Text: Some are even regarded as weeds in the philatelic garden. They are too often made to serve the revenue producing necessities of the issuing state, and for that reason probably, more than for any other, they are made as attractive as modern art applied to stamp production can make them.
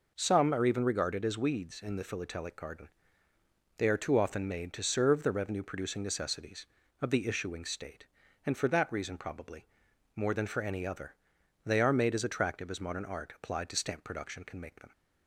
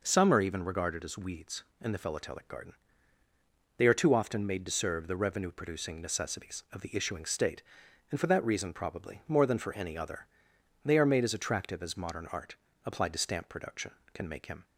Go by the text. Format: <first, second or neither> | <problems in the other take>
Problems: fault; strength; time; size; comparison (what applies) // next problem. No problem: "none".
first | pauses between "art" and "applied"; slight; at 12.5 s; 0.28 s long // says "him" for "them"; at 14.4 s